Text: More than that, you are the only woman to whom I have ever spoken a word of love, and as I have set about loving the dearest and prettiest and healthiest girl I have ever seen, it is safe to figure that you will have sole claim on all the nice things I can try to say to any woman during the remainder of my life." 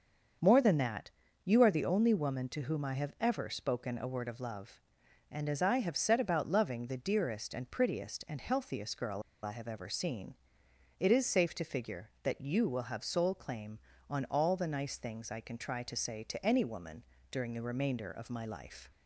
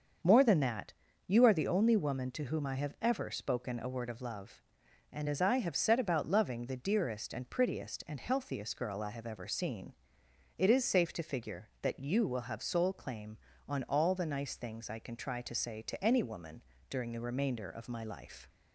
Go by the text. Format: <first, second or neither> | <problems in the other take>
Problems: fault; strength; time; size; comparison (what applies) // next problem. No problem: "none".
second | starts louder than the rest; until 1.7 s; 6.5 dB; also in the second // pauses between "girl" and "I"; slight; at 9.2 s; 0.22 s long // pauses between "woman" and "during"; slight; at 17.0 s; 0.26 s long; slight in the second